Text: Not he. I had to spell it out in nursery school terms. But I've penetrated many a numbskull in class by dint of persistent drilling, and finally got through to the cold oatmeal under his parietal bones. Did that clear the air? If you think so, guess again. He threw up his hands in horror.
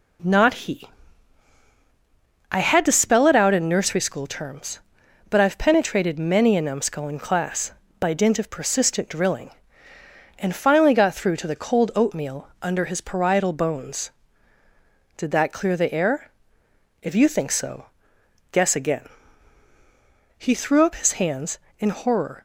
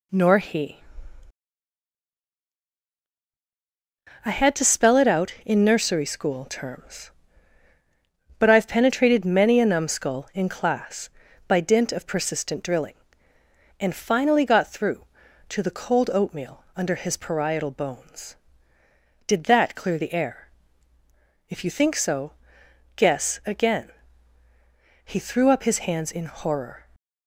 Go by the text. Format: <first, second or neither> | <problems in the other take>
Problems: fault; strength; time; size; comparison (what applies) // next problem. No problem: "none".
first | says "Nor" for "Not"; at 0.1 s